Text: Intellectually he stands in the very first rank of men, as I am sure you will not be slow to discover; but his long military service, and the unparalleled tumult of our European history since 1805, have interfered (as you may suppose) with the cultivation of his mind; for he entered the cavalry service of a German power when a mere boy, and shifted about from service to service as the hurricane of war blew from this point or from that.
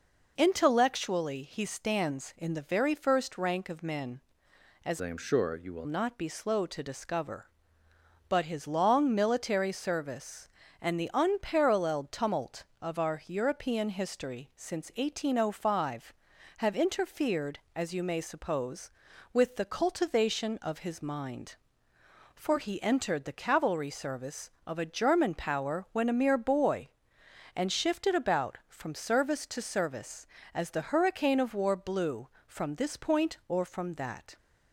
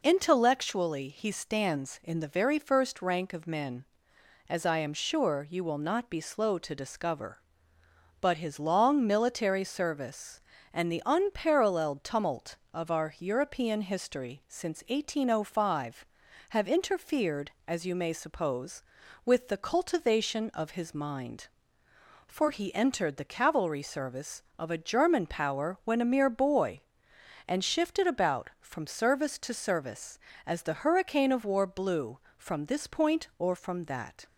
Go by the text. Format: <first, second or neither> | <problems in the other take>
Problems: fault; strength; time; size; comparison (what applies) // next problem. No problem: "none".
second | changes voice from "I" to "will"; from 4.9 to 5.8 s; 0.9 s long